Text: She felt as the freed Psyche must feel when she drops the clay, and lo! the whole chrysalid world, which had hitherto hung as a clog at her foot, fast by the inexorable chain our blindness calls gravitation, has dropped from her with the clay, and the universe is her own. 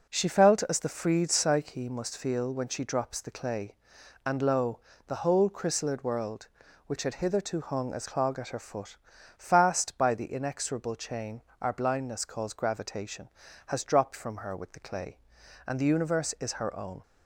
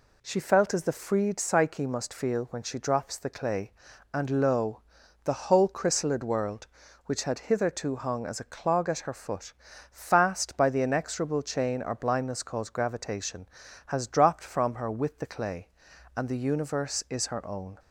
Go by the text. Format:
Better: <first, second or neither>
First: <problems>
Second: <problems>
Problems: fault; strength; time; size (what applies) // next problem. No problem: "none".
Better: second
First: skips "a"; at 8.0 s // pauses between "chain" and "our"; slight; at 11.4 s; 0.22 s long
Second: none